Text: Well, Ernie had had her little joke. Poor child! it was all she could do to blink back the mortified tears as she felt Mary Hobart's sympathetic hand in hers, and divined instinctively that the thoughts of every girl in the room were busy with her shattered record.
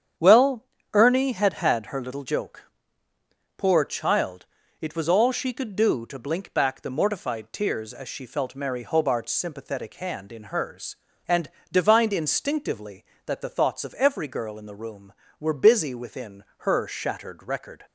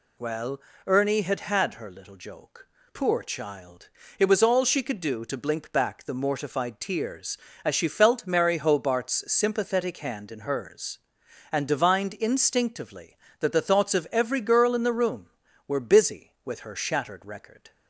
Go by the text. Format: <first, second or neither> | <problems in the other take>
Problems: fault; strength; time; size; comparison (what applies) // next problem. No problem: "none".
second | starts louder than the rest; strong; until 1.4 s; 8.5 dB // pauses between "and" and "divined"; slight; at 11.4 s; 0.22 s long // says "within" for "with"; at 15.9 s